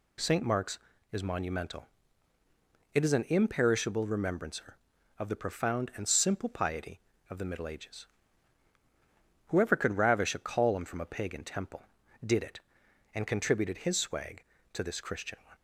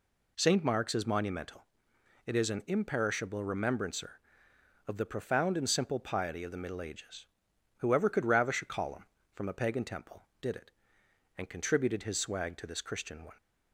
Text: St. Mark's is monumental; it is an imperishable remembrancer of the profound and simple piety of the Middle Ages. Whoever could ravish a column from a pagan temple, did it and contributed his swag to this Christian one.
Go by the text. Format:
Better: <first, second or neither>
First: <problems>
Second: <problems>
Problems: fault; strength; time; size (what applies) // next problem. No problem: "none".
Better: neither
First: none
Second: none